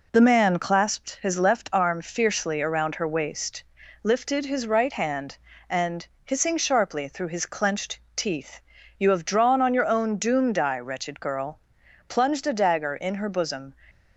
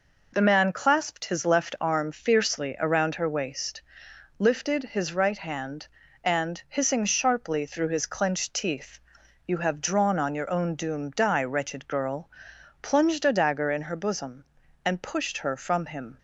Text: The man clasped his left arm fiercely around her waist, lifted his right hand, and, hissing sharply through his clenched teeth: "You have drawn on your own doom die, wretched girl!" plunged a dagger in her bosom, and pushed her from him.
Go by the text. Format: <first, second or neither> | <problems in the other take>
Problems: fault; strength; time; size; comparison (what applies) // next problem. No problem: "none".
second | pauses between "clenched" and "teeth"; slight; at 7.9 s; 0.16 s long // stops before "and pushed her from him"; at 13.8 s